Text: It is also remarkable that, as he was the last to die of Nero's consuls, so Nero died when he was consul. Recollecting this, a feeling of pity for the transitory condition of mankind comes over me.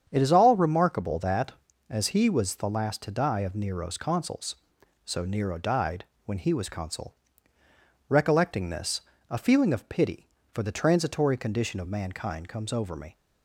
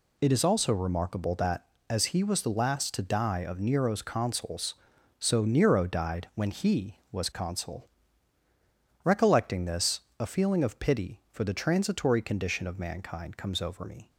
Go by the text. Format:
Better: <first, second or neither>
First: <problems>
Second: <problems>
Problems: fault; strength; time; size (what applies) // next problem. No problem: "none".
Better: second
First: starts louder than the rest; strong; until 1.0 s; 8 dB // says "all" for "also"; at 0.3 s // pauses between "died" and "when"; slight; at 6.0 s; 0.20 s long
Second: none